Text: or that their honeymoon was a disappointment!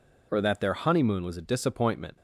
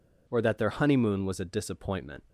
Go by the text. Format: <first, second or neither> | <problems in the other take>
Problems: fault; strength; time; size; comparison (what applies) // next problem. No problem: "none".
neither | none